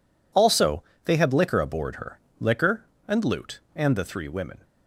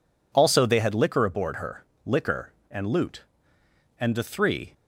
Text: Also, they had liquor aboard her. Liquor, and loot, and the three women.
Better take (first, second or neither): first